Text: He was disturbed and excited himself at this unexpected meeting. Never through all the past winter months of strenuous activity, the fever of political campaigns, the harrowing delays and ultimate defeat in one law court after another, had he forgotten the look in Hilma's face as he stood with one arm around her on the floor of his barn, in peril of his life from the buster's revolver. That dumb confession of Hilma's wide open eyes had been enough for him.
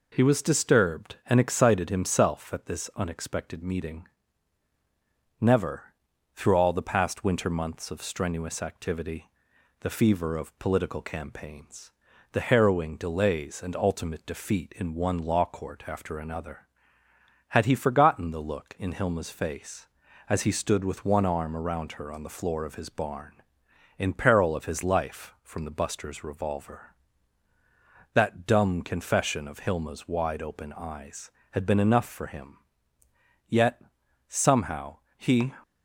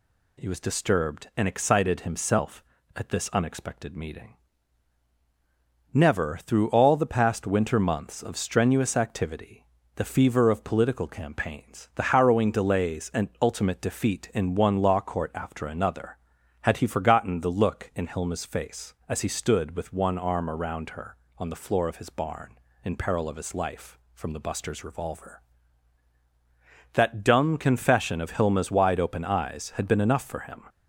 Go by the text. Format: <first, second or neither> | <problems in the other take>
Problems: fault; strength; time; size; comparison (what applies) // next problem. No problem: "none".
second | pauses between "Never" and "through"; at 5.9 s; 0.40 s long // goes on to say "Yet somehow he"; strong; from 33.4 s on; 2.0 s long